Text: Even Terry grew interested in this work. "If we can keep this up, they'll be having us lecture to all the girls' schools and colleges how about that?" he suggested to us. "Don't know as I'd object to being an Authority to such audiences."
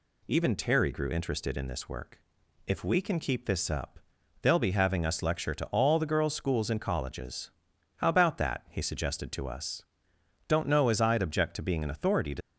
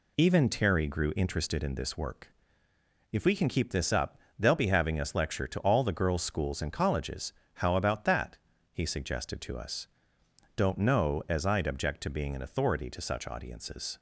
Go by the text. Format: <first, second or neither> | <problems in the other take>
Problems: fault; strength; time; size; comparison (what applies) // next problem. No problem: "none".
second | pauses between "colleges" and "how"; noticeable; at 7.5 s; 0.46 s long; slight in the second // stops before "such audiences"; at 12.4 s